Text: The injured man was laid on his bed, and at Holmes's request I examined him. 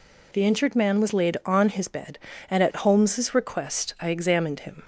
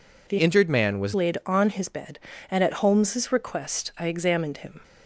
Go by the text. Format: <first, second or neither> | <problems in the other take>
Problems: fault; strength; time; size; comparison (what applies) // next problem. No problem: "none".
first | changes voice from "injured" to "was"; from 0.3 to 1.1 s; 0.8 s long